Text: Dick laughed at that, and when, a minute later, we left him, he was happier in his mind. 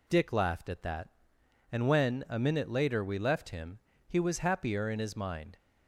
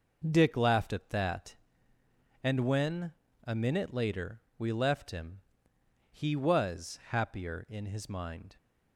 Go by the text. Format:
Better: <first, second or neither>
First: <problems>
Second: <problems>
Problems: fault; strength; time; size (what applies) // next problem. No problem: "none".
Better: neither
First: none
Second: none